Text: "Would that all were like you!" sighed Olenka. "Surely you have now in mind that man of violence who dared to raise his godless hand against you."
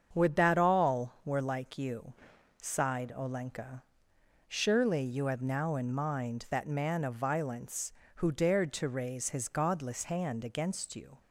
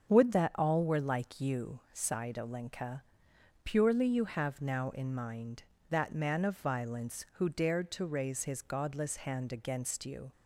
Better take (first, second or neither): first